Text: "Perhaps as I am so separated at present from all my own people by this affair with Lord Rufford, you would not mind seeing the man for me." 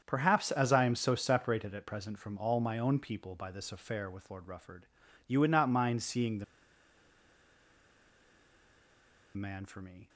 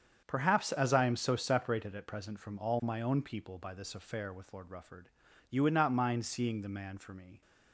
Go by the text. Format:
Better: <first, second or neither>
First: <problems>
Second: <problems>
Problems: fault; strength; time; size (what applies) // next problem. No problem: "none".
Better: second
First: starts louder than the rest; strong; until 1.0 s; 7.5 dB // pauses between "the" and "man"; strong; at 6.4 s; 2.9 s long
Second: starts louder than the rest; strong; until 1.2 s; 7.5 dB